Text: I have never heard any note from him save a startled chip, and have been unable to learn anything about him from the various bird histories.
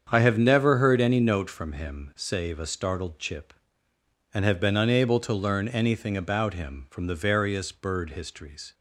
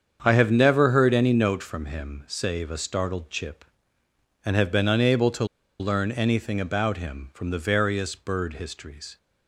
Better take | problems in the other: first | starts louder than the rest; strong; until 1.2 s; 7.5 dB; strong in the first // pauses between "to" and "learn"; slight; at 5.4 s; 0.34 s long

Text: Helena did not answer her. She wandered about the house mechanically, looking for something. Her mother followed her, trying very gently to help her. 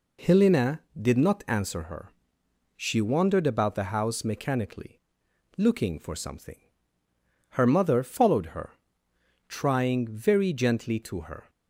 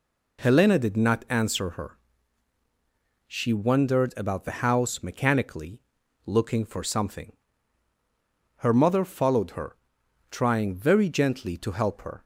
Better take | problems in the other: second | skips "help"; at 11.2 s

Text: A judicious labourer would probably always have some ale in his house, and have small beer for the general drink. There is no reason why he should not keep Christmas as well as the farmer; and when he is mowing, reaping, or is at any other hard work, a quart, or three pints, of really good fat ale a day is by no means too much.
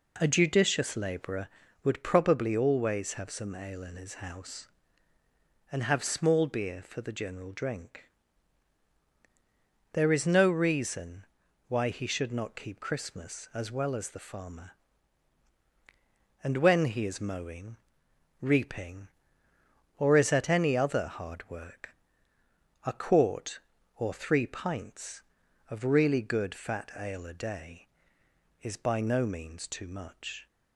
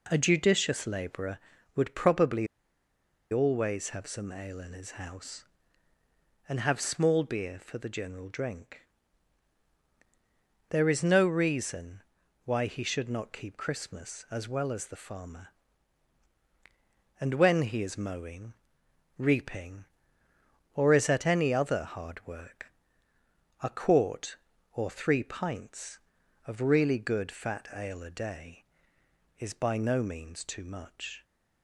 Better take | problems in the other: first | pauses between "probably" and "always"; noticeable; at 2.4 s; 0.84 s long // pauses between "reason" and "why"; at 12.0 s; 0.42 s long; also in the first

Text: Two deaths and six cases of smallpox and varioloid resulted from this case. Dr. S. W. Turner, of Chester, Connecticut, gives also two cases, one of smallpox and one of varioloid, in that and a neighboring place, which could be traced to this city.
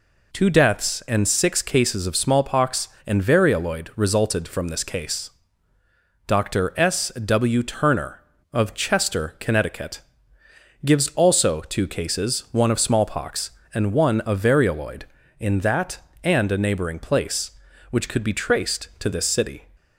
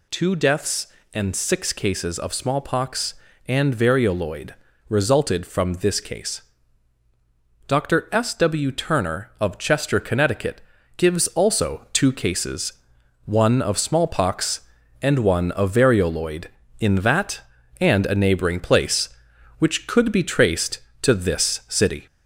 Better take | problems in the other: first | gets louder; slight; throughout; 2.5 dB // pauses between "varioloid" and "resulted"; slight; at 4.5 s; 0.34 s long

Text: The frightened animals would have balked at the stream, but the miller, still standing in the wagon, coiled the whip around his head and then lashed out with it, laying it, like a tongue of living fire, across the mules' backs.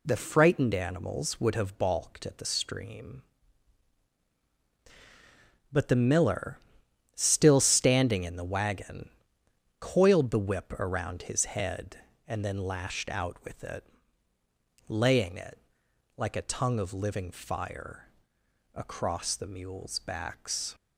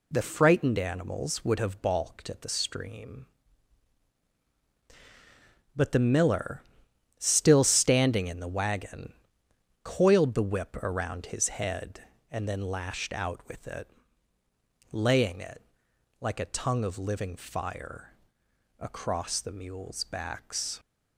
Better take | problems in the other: neither | none

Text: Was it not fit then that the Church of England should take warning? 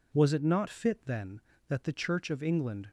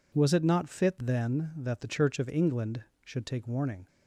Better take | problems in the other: second | stops before "should take warning"; at 2.8 s

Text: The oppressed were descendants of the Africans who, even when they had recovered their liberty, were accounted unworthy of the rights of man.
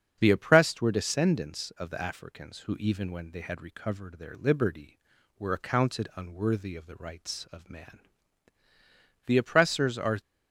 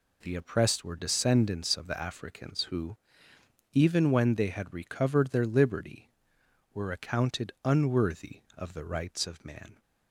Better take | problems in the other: second | starts louder than the rest; strong; until 1.2 s; 7.5 dB // goes on to say "The oppressors are"; noticeable; from 9.2 s on; 0.92 s long

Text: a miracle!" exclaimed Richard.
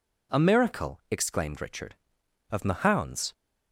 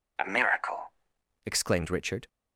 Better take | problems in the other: second | goes on to say "Of Mahound's"; noticeable; from 2.5 s on; 0.82 s long

